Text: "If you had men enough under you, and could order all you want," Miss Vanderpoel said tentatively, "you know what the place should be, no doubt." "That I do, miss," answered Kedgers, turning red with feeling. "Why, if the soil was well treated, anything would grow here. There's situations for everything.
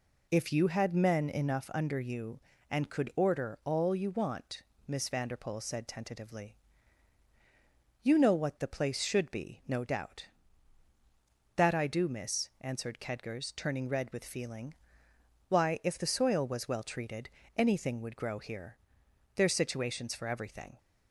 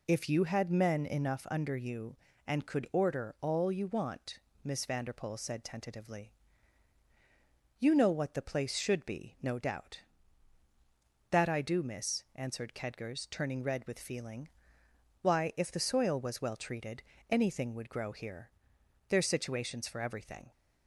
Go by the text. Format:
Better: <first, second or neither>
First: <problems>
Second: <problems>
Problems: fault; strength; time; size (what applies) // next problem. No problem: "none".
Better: neither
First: none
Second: none